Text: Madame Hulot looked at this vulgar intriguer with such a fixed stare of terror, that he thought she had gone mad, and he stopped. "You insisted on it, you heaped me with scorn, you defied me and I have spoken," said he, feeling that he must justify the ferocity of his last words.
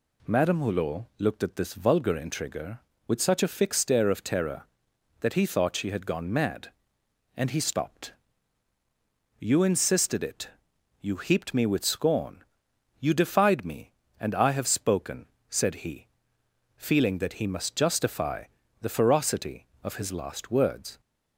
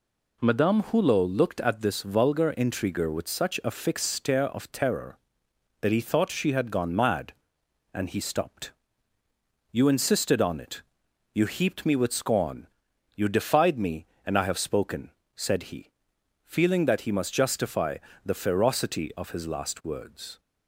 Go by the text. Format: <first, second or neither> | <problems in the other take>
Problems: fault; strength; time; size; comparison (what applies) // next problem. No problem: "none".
second | skips "on"; at 10.2 s // pauses between "justify" and "the"; at 18.4 s; 0.37 s long; slight in the second